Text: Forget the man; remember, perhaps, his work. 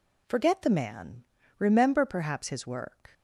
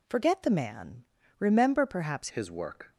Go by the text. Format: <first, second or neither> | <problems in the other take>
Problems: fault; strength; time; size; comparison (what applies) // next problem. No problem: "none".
first | changes voice at "his"; from 2.2 s on; 0.7 s long